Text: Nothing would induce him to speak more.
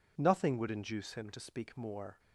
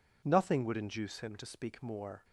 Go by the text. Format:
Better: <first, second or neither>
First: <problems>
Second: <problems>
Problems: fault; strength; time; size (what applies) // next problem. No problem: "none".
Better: neither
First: none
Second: none